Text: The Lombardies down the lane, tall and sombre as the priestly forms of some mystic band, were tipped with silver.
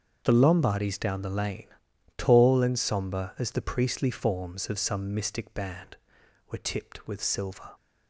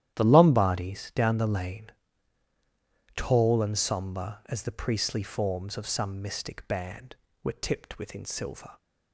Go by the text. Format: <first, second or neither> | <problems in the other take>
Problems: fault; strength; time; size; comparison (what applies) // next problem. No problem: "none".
first | starts louder than the rest; strong; until 1.1 s; 11.5 dB; also in the first // says "within" for "with"; at 7.9 s